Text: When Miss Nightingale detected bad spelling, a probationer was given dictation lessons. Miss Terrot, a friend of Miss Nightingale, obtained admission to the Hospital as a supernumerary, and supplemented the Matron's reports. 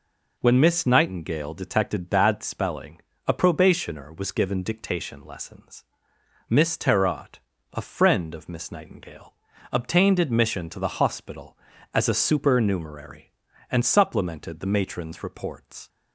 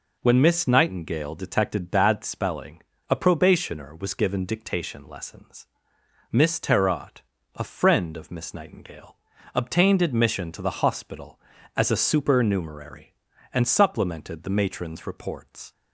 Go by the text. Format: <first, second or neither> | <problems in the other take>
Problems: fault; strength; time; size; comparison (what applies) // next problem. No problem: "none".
neither | none